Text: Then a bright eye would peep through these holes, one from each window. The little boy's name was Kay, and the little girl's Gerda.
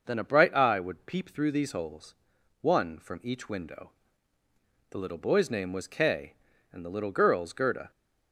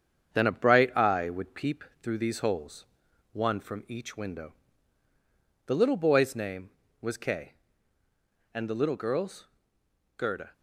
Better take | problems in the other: first | gets quieter; slight; throughout; 3 dB // pauses between "peep" and "through"; slight; at 1.8 s; 0.18 s long // pauses between "girl's" and "Gerda"; noticeable; at 9.4 s; 0.70 s long

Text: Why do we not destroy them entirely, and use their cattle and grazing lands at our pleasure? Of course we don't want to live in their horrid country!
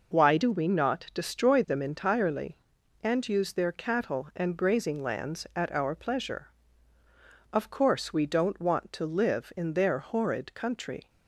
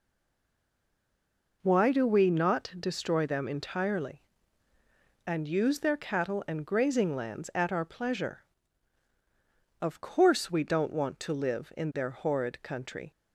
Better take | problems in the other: first | stays silent before the first word; noticeable; until 1.6 s; 1.6 s long

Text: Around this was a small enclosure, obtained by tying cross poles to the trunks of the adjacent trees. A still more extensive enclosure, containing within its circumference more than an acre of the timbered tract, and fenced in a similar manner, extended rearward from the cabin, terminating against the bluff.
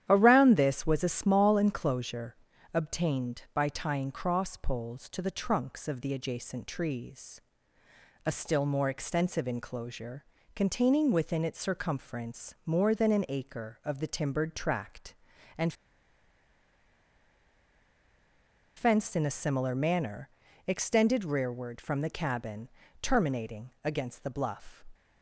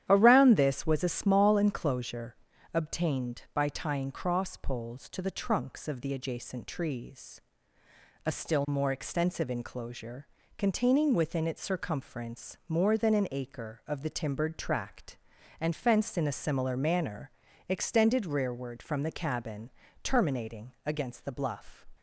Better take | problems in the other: second | starts louder than the rest; strong; until 1.0 s; 10.5 dB; strong in the second // pauses between "and" and "fenced"; strong; at 15.7 s; 3.0 s long // pauses between "terminating" and "against"; slight; at 23.6 s; 0.16 s long; slight in the second

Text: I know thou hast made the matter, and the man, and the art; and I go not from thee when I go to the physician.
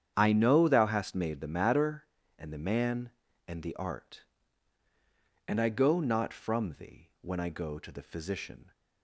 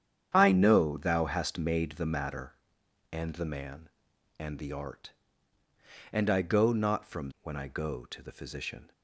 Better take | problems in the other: first | starts louder than the rest; strong; until 1.3 s; 8.5 dB; strong in the first // skips "thee"; at 7.3 s

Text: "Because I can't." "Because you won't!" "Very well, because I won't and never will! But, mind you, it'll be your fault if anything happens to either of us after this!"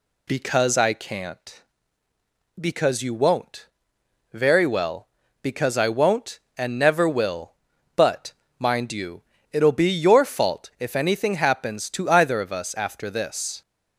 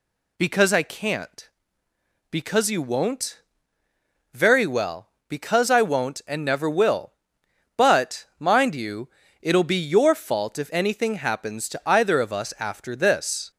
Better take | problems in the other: neither | none

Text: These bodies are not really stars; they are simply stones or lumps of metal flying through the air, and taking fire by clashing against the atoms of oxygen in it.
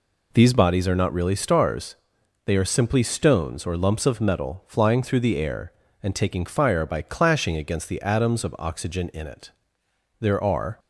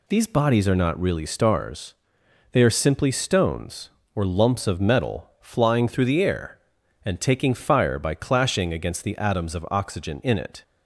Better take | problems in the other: second | goes on to say "There are"; from 10.2 s on; 0.58 s long

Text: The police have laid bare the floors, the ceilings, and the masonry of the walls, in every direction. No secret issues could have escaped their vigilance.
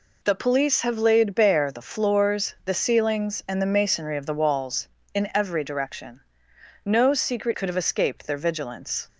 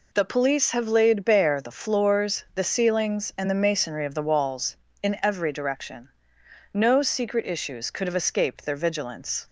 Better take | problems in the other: second | skips "issues"; at 7.5 s

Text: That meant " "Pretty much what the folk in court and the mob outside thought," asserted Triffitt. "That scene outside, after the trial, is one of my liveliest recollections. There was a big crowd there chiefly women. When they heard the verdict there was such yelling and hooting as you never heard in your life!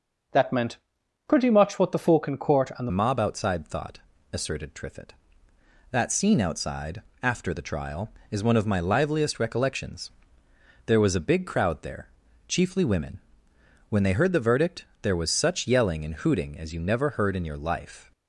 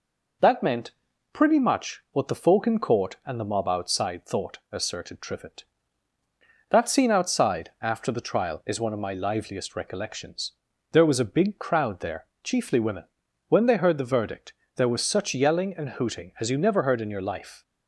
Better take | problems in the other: second | changes voice at "mob"; from 2.9 s on; 15.2 s long // pauses between "there" and "chiefly"; at 12.0 s; 0.38 s long; slight in the second // pauses between "verdict" and "there"; slight; at 14.8 s; 0.16 s long; slight in the second

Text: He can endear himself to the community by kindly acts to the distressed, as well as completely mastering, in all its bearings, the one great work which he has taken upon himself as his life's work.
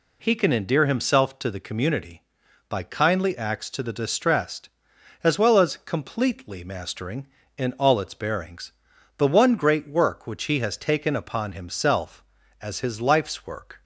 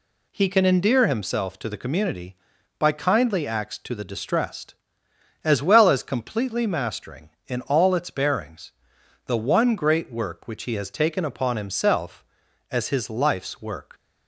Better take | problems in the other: neither | none

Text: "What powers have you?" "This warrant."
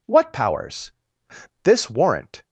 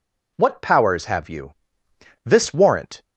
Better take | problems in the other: second | skips "have you"; at 1.2 s

